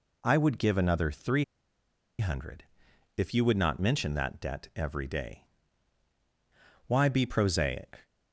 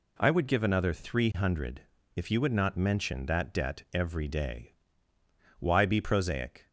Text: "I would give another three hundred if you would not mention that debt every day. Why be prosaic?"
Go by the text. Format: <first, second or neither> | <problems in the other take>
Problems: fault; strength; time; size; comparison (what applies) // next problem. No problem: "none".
second | pauses between "three" and "hundred"; noticeable; at 1.4 s; 0.74 s long // pauses between "hundred" and "if"; noticeable; at 2.6 s; 0.54 s long; slight in the second